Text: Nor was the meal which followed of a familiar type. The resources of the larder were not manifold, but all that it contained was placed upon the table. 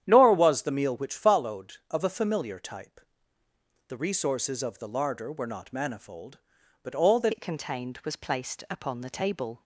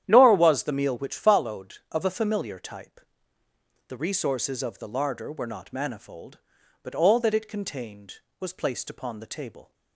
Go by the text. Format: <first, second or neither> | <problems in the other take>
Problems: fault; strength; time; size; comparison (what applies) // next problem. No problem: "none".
second | starts louder than the rest; strong; until 1.0 s; 10 dB; strong in the second // changes voice at "it"; from 7.3 s on; 2.3 s long